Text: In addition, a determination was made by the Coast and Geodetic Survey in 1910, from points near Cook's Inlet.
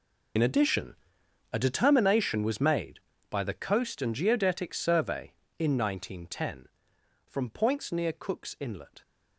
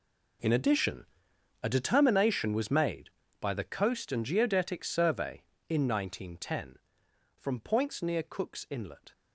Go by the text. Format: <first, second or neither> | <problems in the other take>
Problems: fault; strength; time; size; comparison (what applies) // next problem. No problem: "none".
second | loses the start of "In"; at 0.3 s; 55 ms